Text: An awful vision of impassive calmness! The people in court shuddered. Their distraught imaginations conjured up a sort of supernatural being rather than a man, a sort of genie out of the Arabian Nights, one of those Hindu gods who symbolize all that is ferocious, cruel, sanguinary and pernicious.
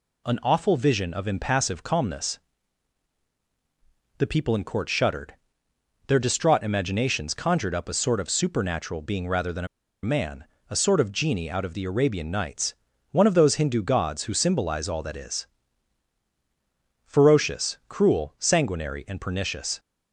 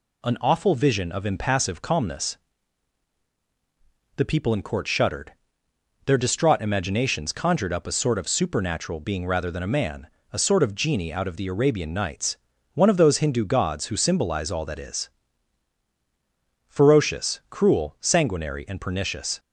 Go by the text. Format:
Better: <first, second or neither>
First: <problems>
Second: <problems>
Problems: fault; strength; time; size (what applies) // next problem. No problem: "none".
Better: second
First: pauses between "a" and "man"; at 9.6 s; 0.37 s long // pauses between "is" and "ferocious"; strong; at 15.4 s; 1.5 s long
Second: pauses between "is" and "ferocious"; strong; at 15.0 s; 1.5 s long